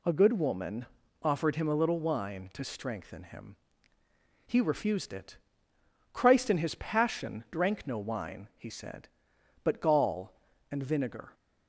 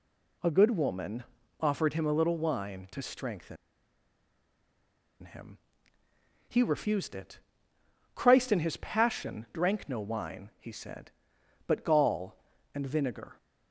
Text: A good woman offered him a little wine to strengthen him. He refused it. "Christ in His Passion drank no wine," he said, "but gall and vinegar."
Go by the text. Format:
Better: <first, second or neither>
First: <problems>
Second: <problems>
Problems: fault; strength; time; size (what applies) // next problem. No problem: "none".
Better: first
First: pauses between "woman" and "offered"; slight; at 0.8 s; 0.34 s long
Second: pauses between "woman" and "offered"; slight; at 1.2 s; 0.34 s long // pauses between "strengthen" and "him"; strong; at 3.5 s; 1.6 s long